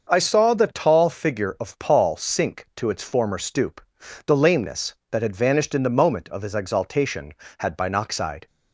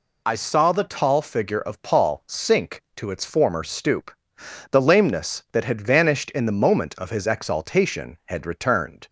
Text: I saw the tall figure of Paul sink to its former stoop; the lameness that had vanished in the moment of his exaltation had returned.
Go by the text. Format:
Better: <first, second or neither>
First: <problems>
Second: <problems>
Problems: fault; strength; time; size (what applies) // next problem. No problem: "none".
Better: second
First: starts louder than the rest; until 1.1 s; 6.5 dB // says "binoxide" for "returned"; at 7.7 s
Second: none